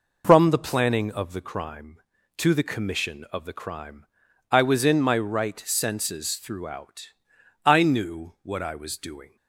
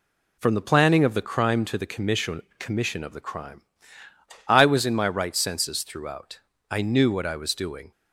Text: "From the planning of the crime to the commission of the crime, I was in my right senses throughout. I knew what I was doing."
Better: first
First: none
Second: says "commission" twice; at 2.5 s

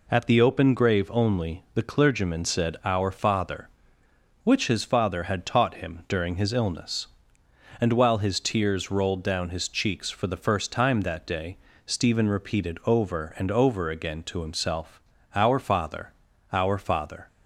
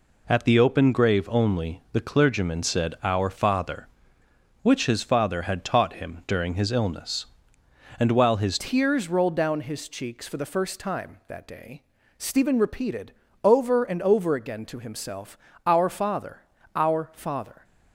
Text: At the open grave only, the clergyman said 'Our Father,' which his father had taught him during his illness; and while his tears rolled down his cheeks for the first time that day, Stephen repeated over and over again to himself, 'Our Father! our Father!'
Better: first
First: none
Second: changes voice at "tears"; from 8.5 s on; 9.1 s long // pauses between "repeated" and "over"; slight; at 13.1 s; 0.32 s long

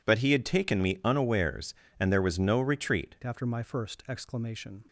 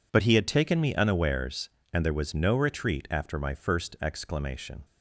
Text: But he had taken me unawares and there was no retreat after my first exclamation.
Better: second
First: changes voice at "after"; from 3.2 s on; 1.6 s long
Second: none

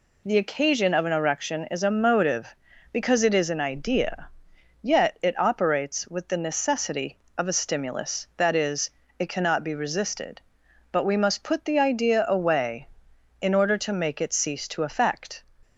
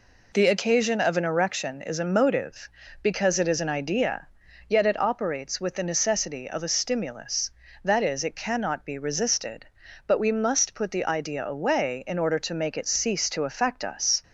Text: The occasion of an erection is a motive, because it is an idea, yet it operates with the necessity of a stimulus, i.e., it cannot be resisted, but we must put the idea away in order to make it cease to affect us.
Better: second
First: stops before "us"; at 15.6 s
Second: none

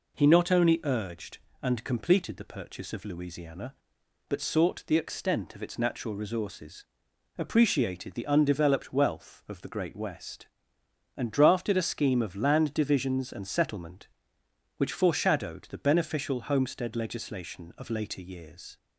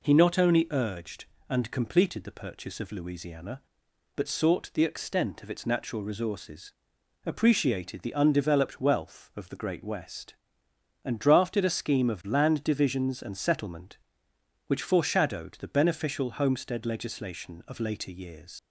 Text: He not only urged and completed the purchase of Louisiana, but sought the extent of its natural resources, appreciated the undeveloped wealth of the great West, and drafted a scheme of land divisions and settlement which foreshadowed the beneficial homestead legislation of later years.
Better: first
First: none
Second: leaves "years" unfinished; at 18.5 s; 75 ms

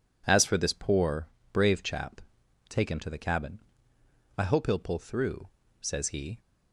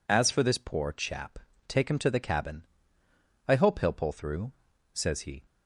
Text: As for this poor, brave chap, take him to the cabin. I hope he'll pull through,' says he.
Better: first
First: none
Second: skips "brave"; at 0.9 s

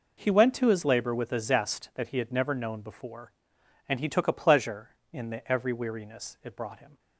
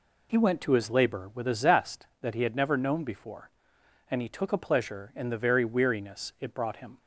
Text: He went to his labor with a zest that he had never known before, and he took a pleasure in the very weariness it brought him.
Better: second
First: says "every" for "very"; at 5.4 s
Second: none

